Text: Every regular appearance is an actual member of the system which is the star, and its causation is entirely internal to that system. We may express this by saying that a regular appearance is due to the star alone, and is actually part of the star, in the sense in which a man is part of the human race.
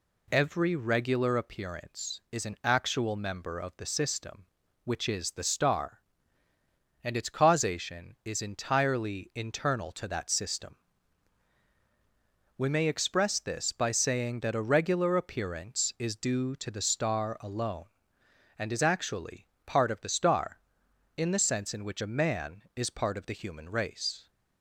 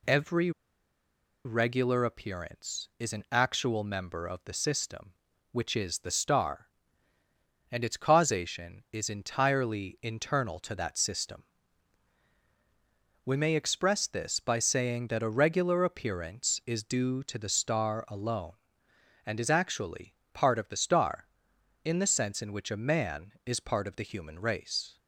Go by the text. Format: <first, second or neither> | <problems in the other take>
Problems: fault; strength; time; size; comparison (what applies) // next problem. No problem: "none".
first | pauses between "Every" and "regular"; noticeable; at 0.5 s; 0.94 s long // pauses between "actually" and "part"; slight; at 20.1 s; 0.18 s long; slight in the first